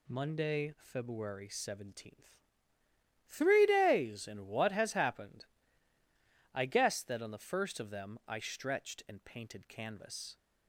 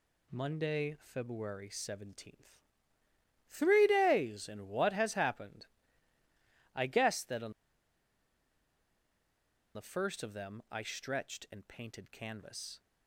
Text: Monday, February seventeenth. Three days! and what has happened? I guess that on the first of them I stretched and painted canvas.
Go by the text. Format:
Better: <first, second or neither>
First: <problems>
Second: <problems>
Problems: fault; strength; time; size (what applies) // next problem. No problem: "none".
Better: first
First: none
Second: pauses between "on" and "the"; strong; at 7.5 s; 2.2 s long